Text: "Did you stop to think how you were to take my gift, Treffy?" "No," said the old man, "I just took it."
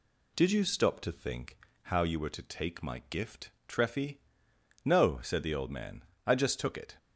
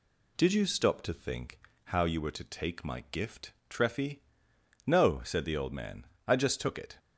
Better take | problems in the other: neither | pauses between "think" and "how"; slight; the same in both

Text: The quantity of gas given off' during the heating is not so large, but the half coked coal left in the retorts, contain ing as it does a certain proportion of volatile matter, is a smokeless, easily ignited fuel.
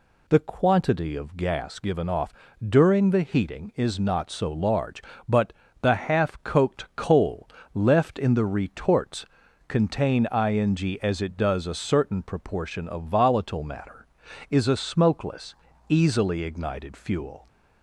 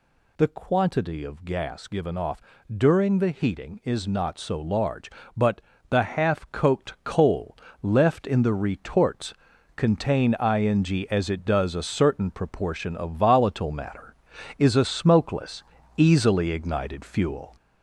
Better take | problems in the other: first | gets louder; throughout; 4 dB // pauses between "off" and "during"; slight; at 2.4 s; 0.34 s long; slight in the first // pauses between "but" and "the"; slight; at 5.6 s; 0.30 s long; slight in the first // pauses between "coal" and "left"; slight; at 7.5 s; 0.28 s long; slight in the first

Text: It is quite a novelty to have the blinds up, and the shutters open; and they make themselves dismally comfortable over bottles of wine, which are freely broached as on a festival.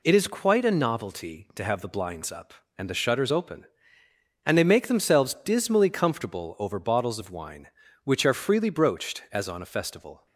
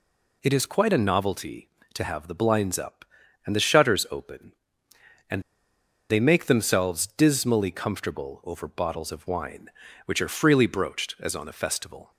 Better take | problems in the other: first | pauses between "and" and "they"; noticeable; at 5.4 s; 0.68 s long

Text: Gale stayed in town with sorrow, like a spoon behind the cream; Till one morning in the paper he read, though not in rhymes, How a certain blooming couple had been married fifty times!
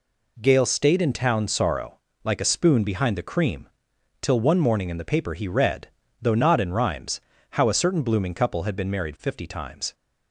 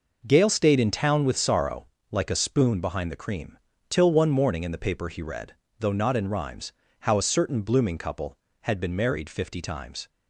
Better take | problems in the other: second | skips "with"; at 1.4 s

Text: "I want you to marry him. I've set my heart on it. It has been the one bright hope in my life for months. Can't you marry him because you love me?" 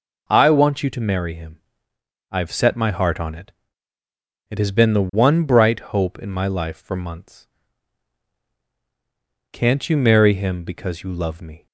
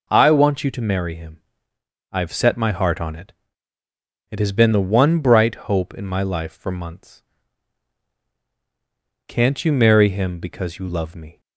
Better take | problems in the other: neither | none

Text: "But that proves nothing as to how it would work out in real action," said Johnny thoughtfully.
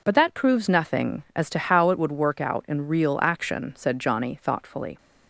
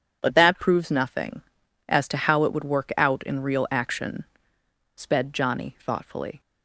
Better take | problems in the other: first | says "sped" for "said"; at 4.9 s

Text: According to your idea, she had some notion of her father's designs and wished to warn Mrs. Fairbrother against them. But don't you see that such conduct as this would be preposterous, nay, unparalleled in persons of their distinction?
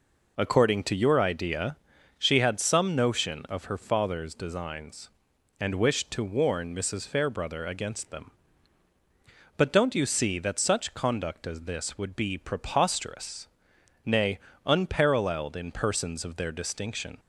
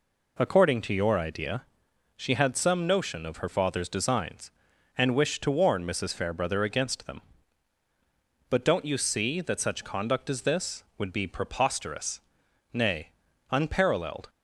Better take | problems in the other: first | stops before "in persons of their distinction"; at 14.2 s

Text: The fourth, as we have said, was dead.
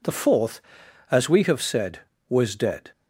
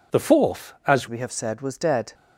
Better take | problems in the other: first | changes voice at "we"; from 1.0 s on; 1.1 s long

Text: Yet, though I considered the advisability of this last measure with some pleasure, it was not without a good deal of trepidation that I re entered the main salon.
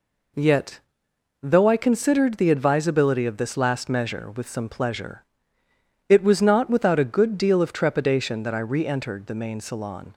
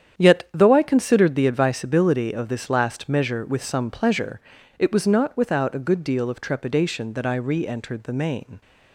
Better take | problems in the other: first | starts louder than the rest; strong; until 1.1 s; 8.5 dB // stops before "salon"; at 8.6 s

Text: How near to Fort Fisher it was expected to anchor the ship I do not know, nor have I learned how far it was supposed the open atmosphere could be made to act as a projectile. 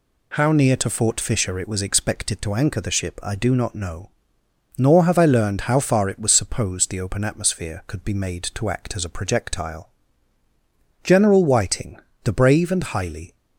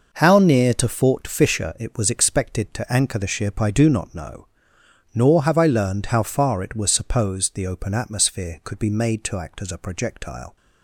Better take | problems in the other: second | goes on to say "General Whiting the brave and highly"; strong; from 11.0 s on; 2.3 s long

